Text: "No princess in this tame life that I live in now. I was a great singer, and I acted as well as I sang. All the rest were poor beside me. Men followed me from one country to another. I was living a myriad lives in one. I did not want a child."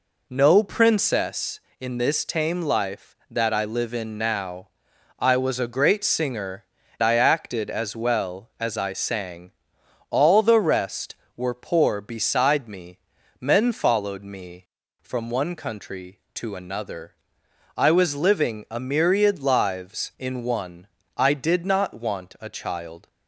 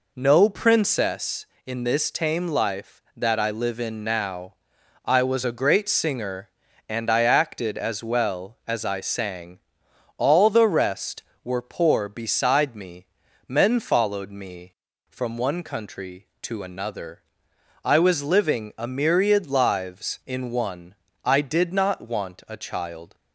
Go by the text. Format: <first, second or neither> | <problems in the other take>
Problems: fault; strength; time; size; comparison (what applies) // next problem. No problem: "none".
second | skips "and"; at 6.8 s